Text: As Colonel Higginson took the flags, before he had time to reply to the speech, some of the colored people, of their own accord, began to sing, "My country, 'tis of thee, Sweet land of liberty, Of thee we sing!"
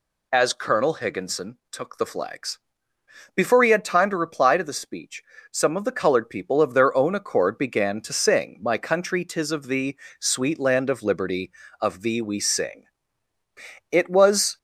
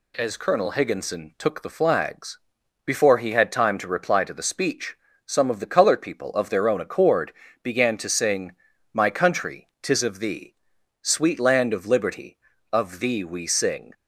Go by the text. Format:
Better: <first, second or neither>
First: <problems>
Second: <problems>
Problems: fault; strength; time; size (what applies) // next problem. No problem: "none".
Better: second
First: goes on to say "It was"; noticeable; from 13.9 s on; 0.66 s long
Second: none